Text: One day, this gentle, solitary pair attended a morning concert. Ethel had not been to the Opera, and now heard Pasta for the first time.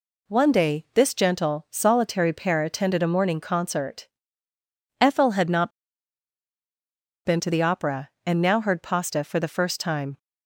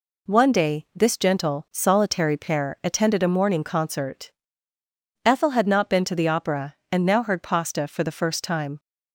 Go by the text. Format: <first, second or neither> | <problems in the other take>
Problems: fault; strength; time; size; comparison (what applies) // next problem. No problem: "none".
second | pauses between "not" and "been"; strong; at 5.6 s; 1.5 s long